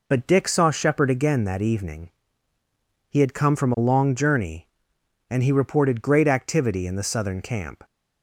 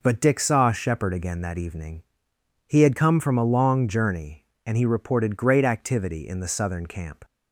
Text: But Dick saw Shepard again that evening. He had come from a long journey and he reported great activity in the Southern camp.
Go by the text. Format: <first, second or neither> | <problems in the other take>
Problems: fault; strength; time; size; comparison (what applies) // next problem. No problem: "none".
neither | none